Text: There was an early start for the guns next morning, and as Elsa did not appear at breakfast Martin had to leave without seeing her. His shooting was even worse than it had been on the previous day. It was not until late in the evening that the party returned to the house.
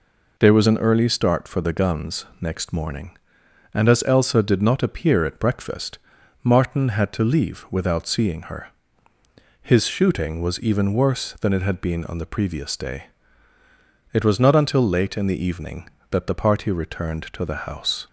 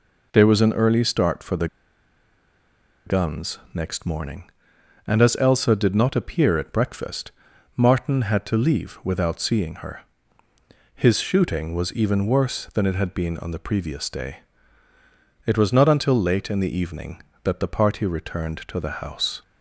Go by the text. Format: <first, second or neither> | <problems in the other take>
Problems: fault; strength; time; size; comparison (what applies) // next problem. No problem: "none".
first | pauses between "the" and "guns"; strong; at 1.6 s; 1.4 s long // pauses between "guns" and "next"; slight; at 3.5 s; 0.16 s long; slight in the first // pauses between "breakfast" and "Martin"; at 7.3 s; 0.44 s long; also in the first